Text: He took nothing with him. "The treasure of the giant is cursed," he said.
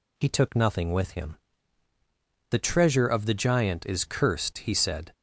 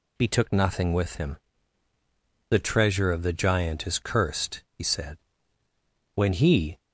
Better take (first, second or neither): first